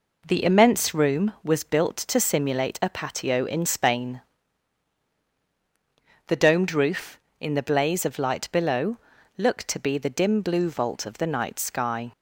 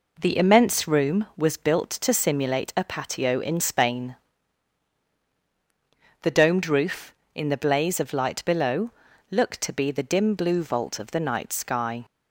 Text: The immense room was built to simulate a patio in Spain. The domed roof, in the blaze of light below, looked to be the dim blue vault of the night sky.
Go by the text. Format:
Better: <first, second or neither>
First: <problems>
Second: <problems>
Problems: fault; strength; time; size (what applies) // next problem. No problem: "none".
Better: neither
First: none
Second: none